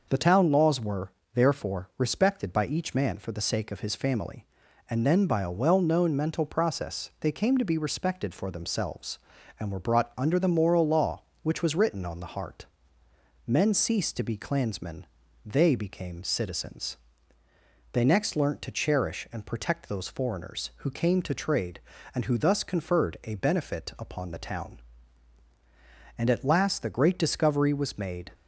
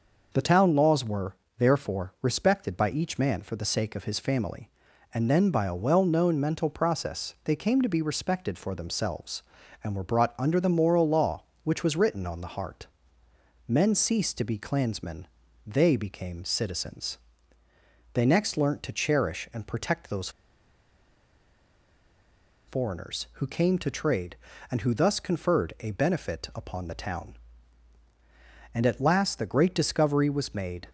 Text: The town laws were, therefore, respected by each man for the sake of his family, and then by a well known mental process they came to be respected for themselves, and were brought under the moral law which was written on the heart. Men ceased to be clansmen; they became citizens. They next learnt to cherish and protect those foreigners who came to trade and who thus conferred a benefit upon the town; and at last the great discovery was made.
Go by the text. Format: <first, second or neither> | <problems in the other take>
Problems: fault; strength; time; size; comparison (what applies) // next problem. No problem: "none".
first | pauses between "those" and "foreigners"; strong; at 20.2 s; 2.3 s long